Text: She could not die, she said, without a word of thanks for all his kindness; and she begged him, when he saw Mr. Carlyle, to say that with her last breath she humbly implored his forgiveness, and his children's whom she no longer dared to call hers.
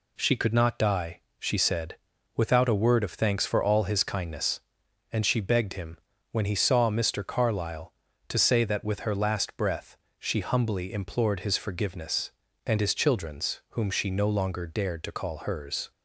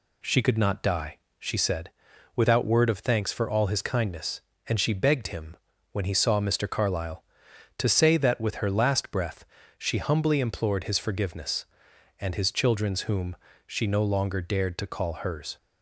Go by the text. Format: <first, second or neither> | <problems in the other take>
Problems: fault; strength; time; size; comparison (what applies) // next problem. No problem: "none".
first | skips "a"; at 2.6 s // pauses between "breath" and "she"; slight; at 9.4 s; 0.32 s long; slight in the first // pauses between "whom" and "she"; slight; at 13.3 s; 0.32 s long